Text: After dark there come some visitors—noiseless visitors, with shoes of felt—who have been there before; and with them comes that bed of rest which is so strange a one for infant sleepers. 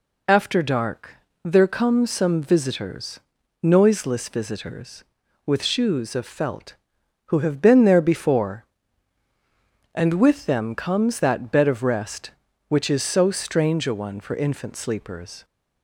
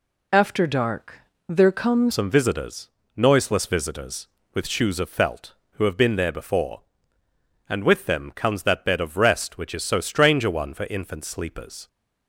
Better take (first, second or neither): first